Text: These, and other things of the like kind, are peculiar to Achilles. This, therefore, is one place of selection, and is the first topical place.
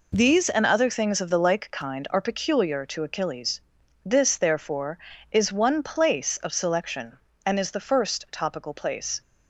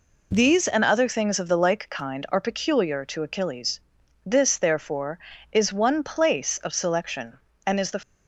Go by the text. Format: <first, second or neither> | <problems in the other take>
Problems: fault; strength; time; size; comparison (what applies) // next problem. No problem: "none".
first | stops before "first topical place"; at 8.0 s